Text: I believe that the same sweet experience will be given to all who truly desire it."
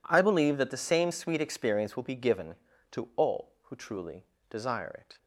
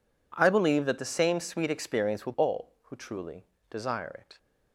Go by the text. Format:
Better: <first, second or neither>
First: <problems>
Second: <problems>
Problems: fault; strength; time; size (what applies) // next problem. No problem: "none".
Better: first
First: pauses between "truly" and "desire"; slight; at 4.2 s; 0.24 s long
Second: skips "be given to"; at 2.3 s // pauses between "truly" and "desire"; slight; at 3.4 s; 0.24 s long